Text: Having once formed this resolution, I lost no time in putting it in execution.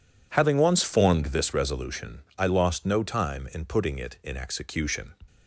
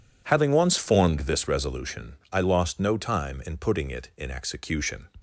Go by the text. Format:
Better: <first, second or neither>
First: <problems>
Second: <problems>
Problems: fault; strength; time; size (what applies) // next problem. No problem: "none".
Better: neither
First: none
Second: none